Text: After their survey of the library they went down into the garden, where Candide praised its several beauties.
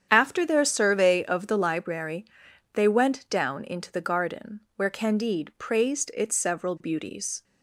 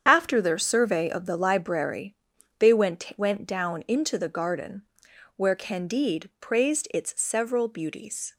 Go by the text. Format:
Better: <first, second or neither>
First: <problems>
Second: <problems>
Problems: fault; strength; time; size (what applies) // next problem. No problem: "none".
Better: first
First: starts louder than the rest; strong; until 1.1 s; 8.5 dB // pauses between "library" and "they"; noticeable; at 2.2 s; 0.50 s long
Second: starts louder than the rest; strong; until 1.0 s; 8 dB // pauses between "library" and "they"; at 2.1 s; 0.44 s long // says "went" twice; at 3.1 s